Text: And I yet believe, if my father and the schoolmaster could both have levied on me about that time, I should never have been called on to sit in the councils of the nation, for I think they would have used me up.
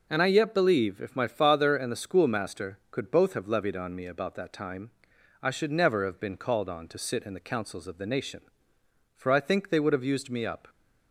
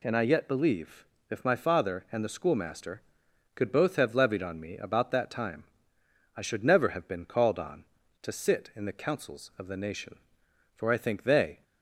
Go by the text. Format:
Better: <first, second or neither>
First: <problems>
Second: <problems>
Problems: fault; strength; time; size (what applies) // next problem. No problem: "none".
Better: first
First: none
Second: stops before "would have used me up"; at 11.6 s